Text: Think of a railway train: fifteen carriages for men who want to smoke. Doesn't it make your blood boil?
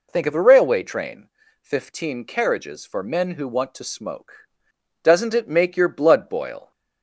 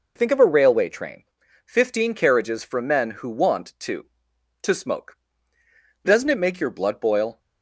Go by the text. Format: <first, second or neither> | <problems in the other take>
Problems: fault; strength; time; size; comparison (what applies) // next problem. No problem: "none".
first | says "to" twice; at 4.6 s